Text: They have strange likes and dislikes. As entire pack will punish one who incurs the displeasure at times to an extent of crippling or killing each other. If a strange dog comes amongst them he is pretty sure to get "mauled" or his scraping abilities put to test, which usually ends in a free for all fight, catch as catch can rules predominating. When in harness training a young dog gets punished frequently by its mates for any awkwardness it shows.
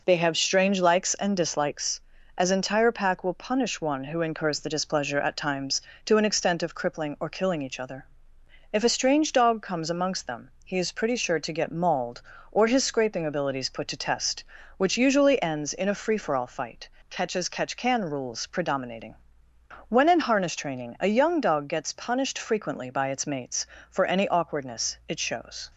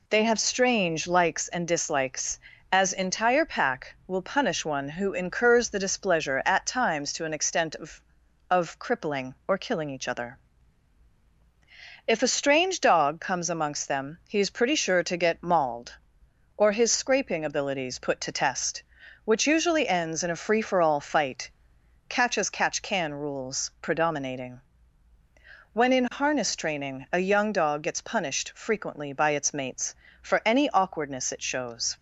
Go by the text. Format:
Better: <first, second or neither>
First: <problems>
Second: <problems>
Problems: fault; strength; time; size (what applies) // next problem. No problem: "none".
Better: first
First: none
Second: says "of" twice; at 8.4 s